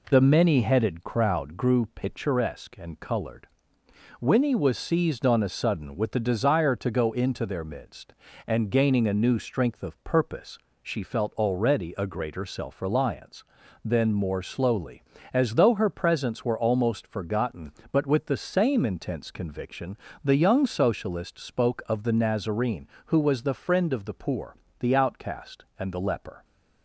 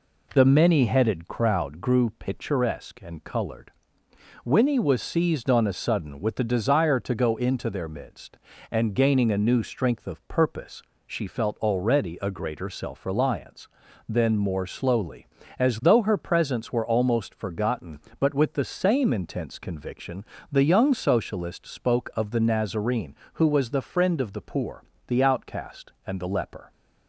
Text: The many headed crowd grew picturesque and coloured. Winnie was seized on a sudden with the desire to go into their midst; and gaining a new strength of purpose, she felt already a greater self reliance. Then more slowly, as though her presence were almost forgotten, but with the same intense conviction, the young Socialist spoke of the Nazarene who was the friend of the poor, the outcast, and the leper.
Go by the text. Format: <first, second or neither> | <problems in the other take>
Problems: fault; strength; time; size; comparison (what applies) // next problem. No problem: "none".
neither | none